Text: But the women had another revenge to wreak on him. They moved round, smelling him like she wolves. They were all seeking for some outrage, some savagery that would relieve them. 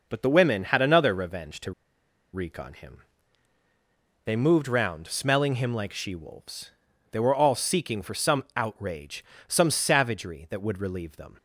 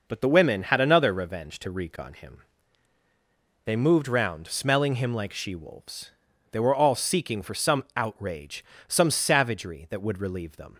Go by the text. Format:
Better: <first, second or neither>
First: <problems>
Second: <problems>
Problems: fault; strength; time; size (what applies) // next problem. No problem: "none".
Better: second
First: pauses between "to" and "wreak"; noticeable; at 1.7 s; 0.61 s long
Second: none